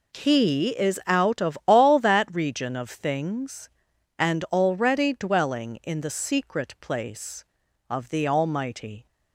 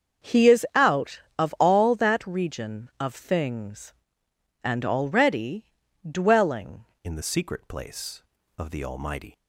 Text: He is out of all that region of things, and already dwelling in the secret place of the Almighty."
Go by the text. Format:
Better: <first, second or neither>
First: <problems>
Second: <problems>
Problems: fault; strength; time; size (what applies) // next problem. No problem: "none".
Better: first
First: none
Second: starts louder than the rest; until 1.4 s; 7 dB // pauses between "already" and "dwelling"; at 5.6 s; 0.44 s long // changes voice at "in"; from 7.0 s on; 2.3 s long